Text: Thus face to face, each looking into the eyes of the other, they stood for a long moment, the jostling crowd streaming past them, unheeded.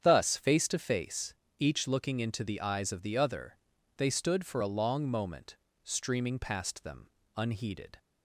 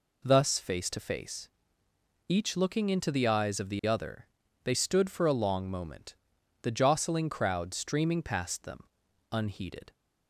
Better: second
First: starts louder than the rest; strong; until 1.0 s; 8.5 dB // skips "the jostling crowd"; at 5.6 s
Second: none

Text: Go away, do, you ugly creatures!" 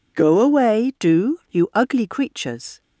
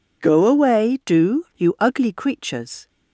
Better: neither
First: none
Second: none

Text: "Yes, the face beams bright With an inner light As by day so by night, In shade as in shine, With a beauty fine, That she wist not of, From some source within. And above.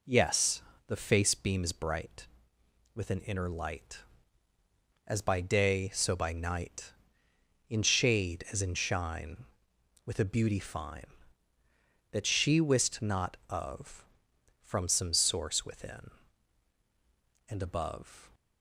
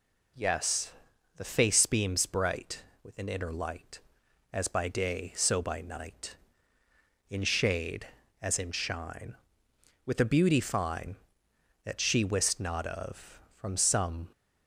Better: first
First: none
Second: stops before "source within And above"; at 14.3 s

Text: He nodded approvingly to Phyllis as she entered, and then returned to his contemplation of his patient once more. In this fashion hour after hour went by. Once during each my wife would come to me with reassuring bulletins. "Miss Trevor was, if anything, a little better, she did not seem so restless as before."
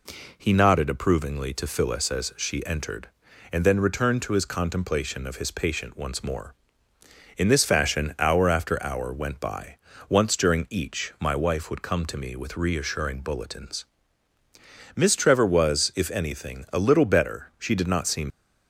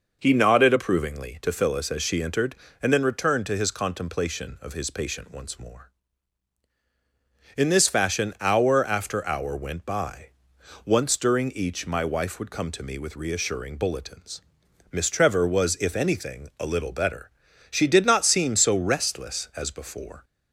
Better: second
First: stops before "so restless as before"; at 18.3 s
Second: none

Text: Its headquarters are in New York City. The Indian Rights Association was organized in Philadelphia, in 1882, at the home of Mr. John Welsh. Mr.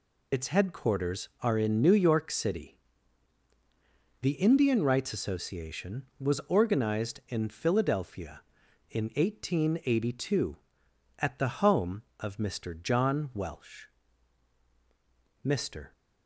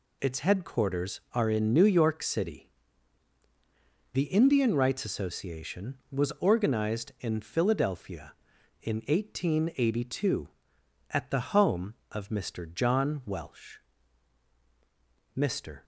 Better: second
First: loses the start of "Its"; at 0.3 s; 25 ms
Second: none

